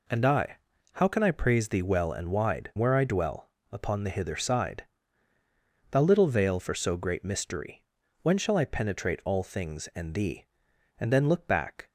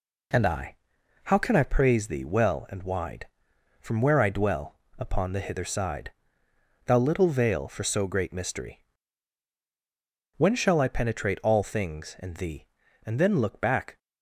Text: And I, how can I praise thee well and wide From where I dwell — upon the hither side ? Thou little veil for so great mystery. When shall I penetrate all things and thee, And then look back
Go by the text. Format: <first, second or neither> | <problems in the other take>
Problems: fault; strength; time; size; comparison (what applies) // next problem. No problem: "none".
second | skips "From"; at 2.7 s